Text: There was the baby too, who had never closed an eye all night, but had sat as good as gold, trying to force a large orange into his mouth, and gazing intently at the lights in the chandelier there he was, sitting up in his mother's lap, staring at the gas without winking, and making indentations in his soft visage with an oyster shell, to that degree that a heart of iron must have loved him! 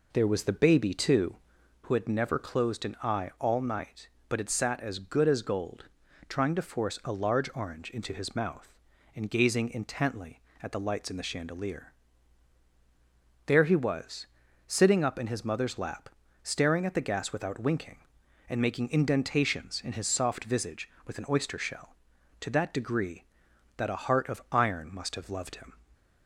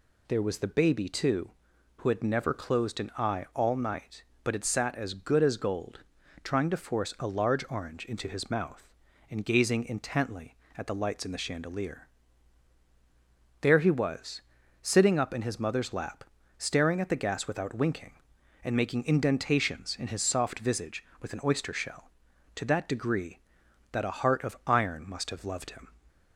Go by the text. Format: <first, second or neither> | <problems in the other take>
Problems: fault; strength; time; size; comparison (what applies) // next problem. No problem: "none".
second | starts louder than the rest; noticeable; until 1.9 s; 4 dB // pauses between "chandelier" and "there"; strong; at 11.9 s; 1.5 s long; strong in the second